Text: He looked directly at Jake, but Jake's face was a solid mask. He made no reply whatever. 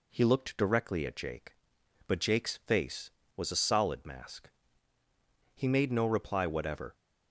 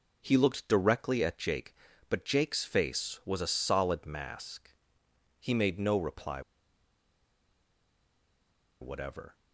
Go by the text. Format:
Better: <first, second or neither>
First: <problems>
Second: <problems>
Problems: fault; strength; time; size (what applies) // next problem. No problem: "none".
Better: first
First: none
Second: pauses between "reply" and "whatever"; strong; at 6.4 s; 2.4 s long